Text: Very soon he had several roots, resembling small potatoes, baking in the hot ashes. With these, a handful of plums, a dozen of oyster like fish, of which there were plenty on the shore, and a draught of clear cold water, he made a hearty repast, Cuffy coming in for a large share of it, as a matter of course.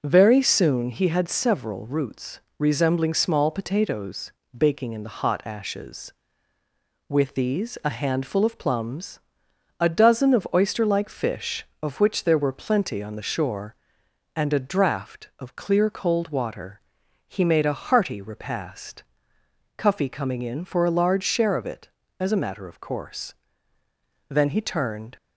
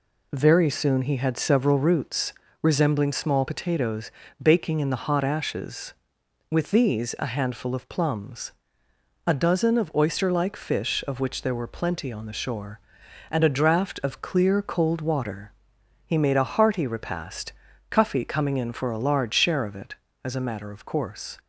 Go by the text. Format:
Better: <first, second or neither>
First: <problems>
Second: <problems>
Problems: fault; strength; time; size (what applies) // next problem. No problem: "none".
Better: second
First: goes on to say "Then he turned"; noticeable; from 24.2 s on; 0.88 s long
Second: none